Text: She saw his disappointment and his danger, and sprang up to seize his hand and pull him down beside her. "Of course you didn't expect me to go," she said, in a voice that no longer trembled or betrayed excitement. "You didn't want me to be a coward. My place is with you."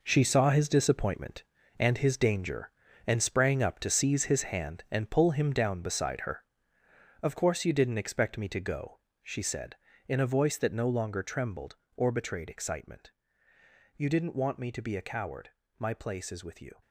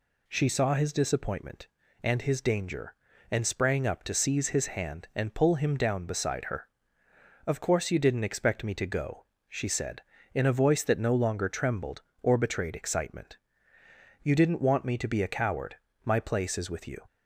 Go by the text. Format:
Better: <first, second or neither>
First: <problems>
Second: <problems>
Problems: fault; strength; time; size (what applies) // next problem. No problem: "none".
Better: second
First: gets quieter; strong; throughout; 10.5 dB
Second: none